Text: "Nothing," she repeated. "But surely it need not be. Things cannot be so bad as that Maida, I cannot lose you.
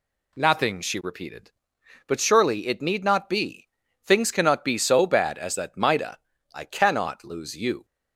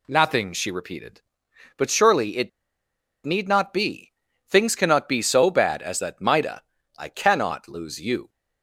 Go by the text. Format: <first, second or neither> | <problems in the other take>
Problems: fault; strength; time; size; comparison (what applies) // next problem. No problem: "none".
first | pauses between "it" and "need"; noticeable; at 2.4 s; 0.74 s long